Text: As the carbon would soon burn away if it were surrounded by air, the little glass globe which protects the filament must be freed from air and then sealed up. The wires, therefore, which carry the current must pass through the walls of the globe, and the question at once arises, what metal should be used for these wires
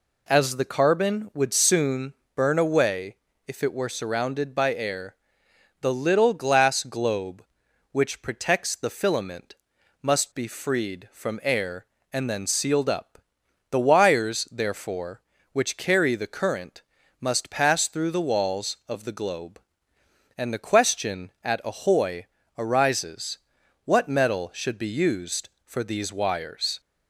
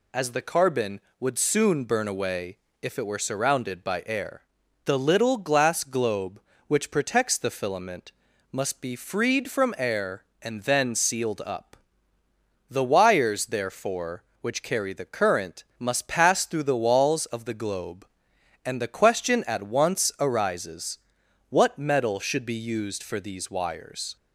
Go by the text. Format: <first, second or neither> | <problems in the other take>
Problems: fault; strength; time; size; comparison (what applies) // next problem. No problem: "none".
second | pauses between "soon" and "burn"; slight; at 2.1 s; 0.22 s long // pauses between "away" and "if"; slight; at 3.1 s; 0.32 s long; slight in the second // pauses between "filament" and "must"; noticeable; at 9.5 s; 0.46 s long; also in the second // pauses between "current" and "must"; at 16.8 s; 0.38 s long // says "ahoy" for "once"; at 21.6 s